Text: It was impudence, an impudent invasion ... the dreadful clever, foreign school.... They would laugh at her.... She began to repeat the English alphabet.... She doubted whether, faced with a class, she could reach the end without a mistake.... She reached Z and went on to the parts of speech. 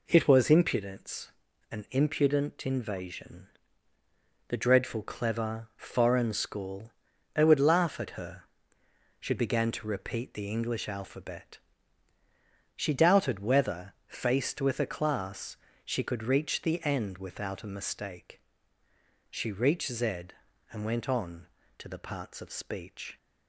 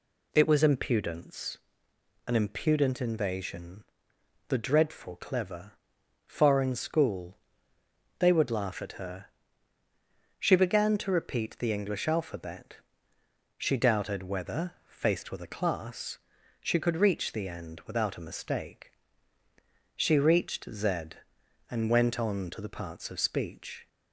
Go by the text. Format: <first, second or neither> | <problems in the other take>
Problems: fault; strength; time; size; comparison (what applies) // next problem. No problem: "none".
neither | none